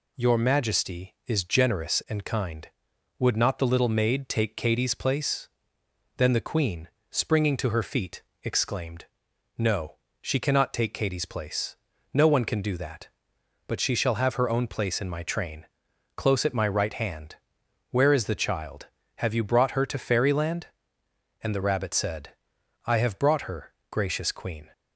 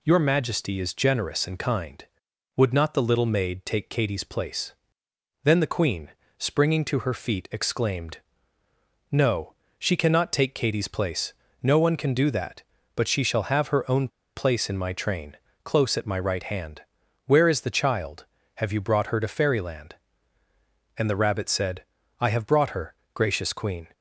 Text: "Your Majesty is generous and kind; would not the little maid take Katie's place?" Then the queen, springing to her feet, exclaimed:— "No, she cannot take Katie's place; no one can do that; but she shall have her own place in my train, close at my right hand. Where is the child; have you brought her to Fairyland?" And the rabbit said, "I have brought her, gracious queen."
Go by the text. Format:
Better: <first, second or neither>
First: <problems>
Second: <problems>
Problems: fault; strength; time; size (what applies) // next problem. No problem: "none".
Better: first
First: none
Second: pauses between "own" and "place"; slight; at 14.0 s; 0.27 s long